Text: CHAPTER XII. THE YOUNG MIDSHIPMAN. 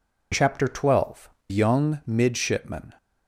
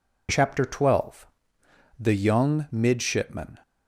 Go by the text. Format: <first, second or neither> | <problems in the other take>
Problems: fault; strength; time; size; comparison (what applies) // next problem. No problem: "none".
second | skips "THE"; at 1.3 s